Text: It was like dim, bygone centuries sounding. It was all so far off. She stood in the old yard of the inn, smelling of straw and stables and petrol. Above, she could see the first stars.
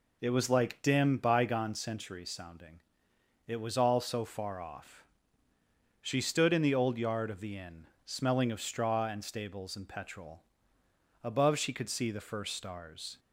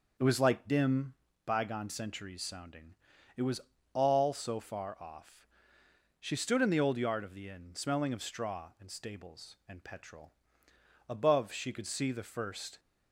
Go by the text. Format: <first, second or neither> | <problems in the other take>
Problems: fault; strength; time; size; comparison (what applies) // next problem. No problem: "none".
first | pauses between "was" and "all"; slight; at 3.5 s; 0.34 s long // stops before "stars"; at 12.7 s